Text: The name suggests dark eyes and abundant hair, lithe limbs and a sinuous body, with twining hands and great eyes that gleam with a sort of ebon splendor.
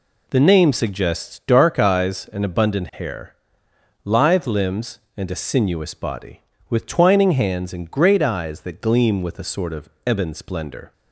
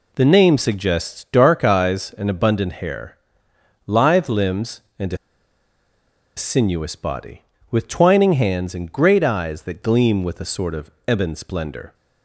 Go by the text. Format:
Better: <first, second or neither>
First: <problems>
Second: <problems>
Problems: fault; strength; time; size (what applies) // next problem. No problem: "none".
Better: first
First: pauses between "of" and "ebon"; slight; at 9.8 s; 0.18 s long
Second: pauses between "a" and "sinuous"; at 5.1 s; 1.2 s long // pauses between "of" and "ebon"; slight; at 10.8 s; 0.18 s long